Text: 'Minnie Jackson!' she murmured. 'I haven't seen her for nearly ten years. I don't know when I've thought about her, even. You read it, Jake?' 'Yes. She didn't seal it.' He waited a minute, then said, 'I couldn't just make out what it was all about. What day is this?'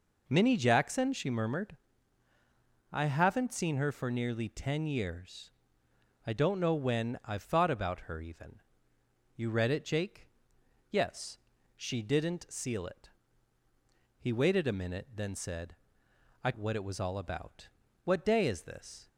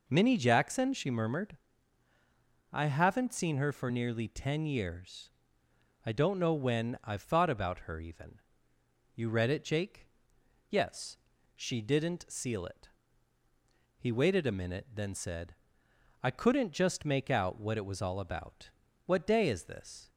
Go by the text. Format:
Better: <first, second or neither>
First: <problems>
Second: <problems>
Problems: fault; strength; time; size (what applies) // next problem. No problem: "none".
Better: second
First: skips "couldn't just make out"; at 16.5 s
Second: none